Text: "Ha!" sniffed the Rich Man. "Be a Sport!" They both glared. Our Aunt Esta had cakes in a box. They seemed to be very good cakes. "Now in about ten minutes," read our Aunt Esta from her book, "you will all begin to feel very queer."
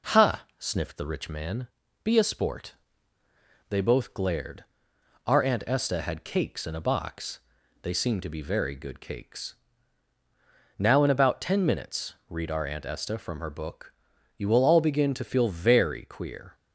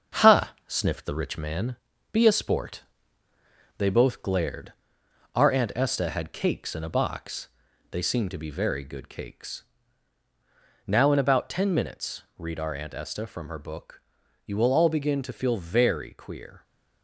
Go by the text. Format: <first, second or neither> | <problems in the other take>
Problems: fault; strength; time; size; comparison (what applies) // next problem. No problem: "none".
first | gets quieter; noticeable; throughout; 5 dB